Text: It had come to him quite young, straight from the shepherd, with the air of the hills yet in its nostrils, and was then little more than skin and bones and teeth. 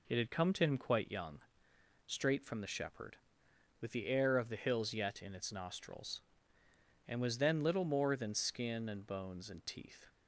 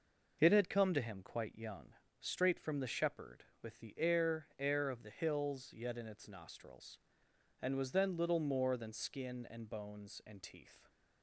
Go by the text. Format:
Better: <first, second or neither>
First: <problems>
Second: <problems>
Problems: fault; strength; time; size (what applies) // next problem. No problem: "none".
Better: first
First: none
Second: says "air" twice; at 4.5 s